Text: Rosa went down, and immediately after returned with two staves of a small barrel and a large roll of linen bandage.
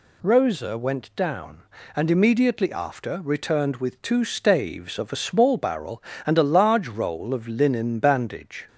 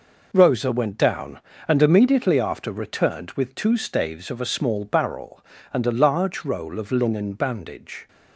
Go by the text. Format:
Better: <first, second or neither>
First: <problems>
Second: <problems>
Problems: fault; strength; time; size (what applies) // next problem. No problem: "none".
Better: neither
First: none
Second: none